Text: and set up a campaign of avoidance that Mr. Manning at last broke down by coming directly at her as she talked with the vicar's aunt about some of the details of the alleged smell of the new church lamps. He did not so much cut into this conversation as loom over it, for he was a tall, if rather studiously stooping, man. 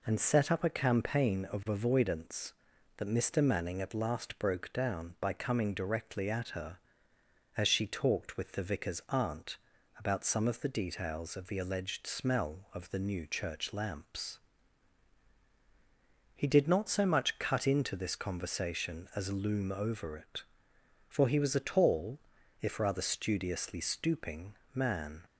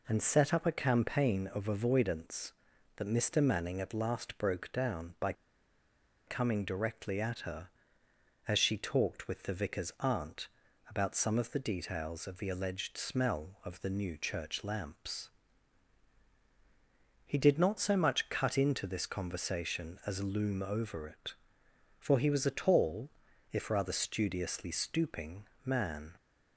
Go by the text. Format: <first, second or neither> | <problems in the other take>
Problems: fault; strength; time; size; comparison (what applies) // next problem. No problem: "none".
first | pauses between "by" and "coming"; noticeable; at 5.3 s; 0.94 s long // pauses between "aunt" and "about"; at 10.4 s; 0.40 s long; also in the first